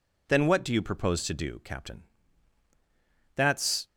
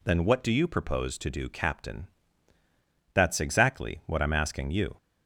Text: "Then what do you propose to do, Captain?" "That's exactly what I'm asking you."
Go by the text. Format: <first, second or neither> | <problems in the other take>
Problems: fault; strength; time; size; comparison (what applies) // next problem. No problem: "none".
second | stops before "exactly what I'm asking you"; at 3.8 s